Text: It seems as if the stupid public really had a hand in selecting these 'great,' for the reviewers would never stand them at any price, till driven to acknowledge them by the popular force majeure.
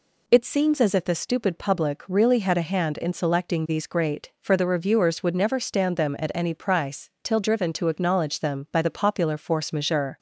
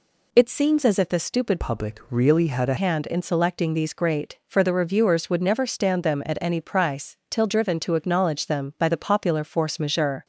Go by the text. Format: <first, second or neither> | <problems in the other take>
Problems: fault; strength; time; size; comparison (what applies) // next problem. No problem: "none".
first | changes voice from "public" to "a"; from 1.5 to 2.7 s; 1.2 s long